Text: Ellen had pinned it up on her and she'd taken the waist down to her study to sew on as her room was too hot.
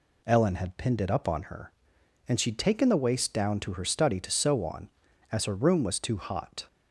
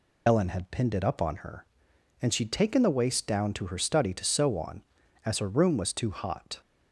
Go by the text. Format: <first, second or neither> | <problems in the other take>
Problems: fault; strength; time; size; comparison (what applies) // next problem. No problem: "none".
first | loses the start of "Ellen"; at 0.2 s; 80 ms